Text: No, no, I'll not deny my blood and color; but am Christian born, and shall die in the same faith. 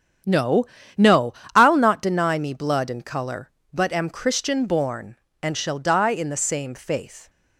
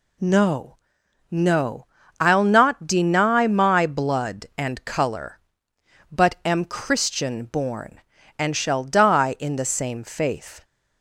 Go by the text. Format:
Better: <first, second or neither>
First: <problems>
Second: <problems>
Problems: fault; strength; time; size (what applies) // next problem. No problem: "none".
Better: second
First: starts louder than the rest; strong; until 1.8 s; 8.5 dB // says "me" for "my"; at 2.3 s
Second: none